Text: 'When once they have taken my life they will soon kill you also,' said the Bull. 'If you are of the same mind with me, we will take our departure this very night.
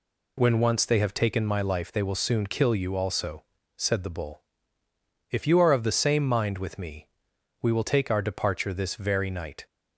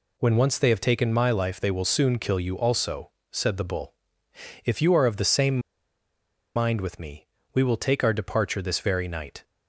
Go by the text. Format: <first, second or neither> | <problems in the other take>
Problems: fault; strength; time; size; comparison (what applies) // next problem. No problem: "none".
first | pauses between "same" and "mind"; noticeable; at 5.5 s; 0.96 s long